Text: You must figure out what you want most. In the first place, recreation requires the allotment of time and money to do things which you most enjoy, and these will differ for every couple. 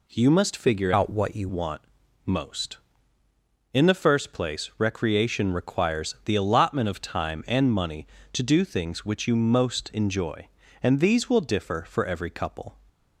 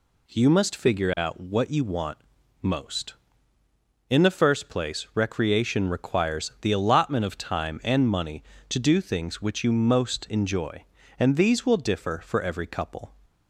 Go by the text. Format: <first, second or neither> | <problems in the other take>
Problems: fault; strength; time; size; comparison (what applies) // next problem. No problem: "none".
second | changes voice from "out" to "you"; from 0.9 to 1.4 s; 0.5 s long // pauses between "want" and "most"; at 1.8 s; 0.44 s long; also in the second